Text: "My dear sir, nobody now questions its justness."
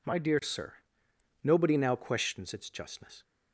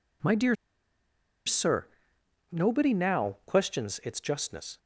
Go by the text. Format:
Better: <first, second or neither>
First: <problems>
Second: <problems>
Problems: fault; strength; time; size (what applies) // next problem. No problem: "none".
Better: first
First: none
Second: pauses between "dear" and "sir"; noticeable; at 0.5 s; 0.91 s long